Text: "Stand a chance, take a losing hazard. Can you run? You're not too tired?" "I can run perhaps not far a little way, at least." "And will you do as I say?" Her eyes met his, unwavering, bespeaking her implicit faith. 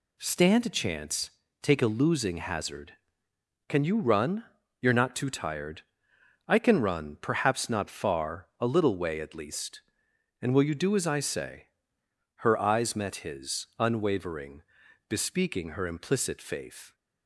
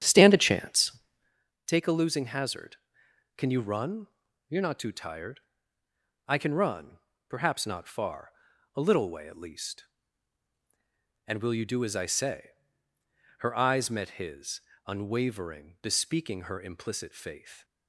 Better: first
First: none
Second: starts louder than the rest; strong; until 1.4 s; 9 dB // pauses between "run" and "perhaps"; slight; at 6.9 s; 0.30 s long // pauses between "far" and "a"; at 8.3 s; 0.42 s long

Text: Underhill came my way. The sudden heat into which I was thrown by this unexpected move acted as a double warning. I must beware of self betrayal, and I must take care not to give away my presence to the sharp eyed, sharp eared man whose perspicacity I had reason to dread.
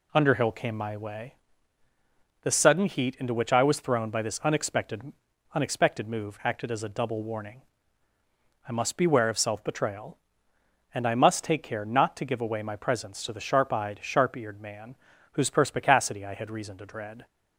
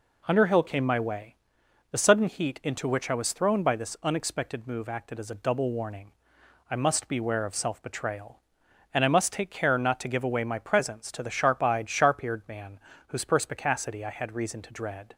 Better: second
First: says "unexpected" twice; at 5.5 s // pauses between "man" and "whose"; at 14.9 s; 0.38 s long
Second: pauses between "man" and "whose"; slight; at 12.7 s; 0.28 s long

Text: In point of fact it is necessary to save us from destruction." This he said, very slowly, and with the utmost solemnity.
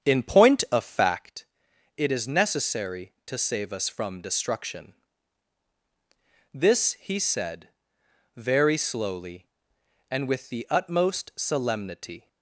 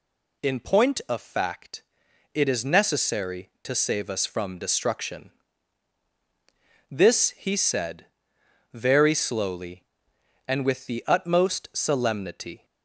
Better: second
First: starts louder than the rest; strong; until 1.4 s; 7.5 dB // pauses between "fact" and "it"; noticeable; at 1.4 s; 0.50 s long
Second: pauses between "fact" and "it"; noticeable; at 1.8 s; 0.50 s long

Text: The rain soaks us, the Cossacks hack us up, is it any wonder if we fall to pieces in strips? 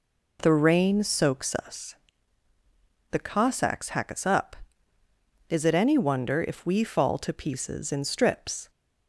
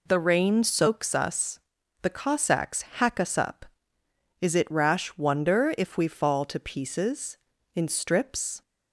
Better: first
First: none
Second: says "rash" for "any"; at 4.7 s

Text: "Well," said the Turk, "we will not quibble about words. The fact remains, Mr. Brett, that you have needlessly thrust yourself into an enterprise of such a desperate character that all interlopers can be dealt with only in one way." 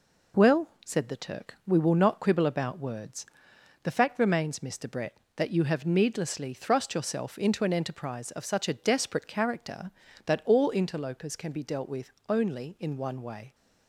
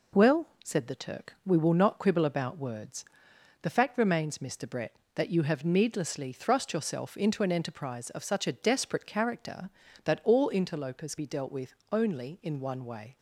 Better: first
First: pauses between "with" and "only"; slight; at 12.1 s; 0.18 s long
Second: skips "can"; at 11.1 s // pauses between "with" and "only"; slight; at 11.7 s; 0.18 s long

